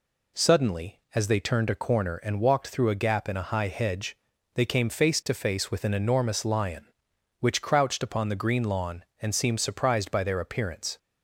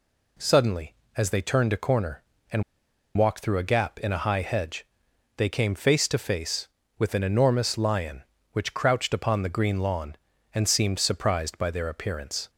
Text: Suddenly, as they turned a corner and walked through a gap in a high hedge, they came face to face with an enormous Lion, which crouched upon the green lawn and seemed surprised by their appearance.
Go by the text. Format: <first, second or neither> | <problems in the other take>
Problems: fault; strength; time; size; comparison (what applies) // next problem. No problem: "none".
first | pauses between "and" and "walked"; noticeable; at 2.6 s; 0.54 s long